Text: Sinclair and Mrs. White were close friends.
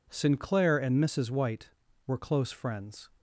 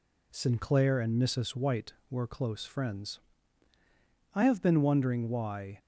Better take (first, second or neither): first